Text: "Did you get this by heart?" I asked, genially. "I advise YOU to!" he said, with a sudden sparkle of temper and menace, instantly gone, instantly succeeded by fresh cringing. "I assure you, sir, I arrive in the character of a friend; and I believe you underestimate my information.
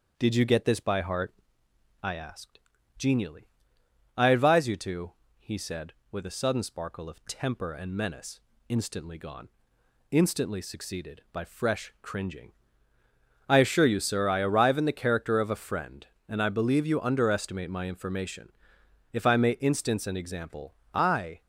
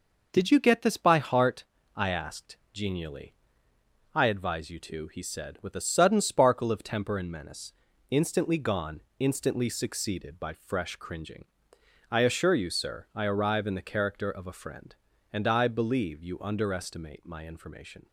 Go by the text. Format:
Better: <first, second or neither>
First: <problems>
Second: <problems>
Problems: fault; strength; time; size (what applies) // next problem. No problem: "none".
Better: second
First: starts louder than the rest; until 1.1 s; 7 dB // goes on to say "If I may instance an example I"; strong; from 19.1 s on; 2.3 s long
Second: none